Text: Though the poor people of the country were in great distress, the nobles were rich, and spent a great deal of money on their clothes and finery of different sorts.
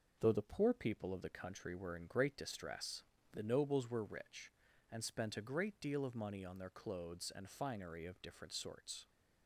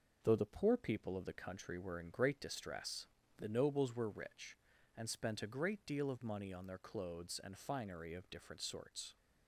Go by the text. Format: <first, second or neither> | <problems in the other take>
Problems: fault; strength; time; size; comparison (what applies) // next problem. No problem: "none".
neither | none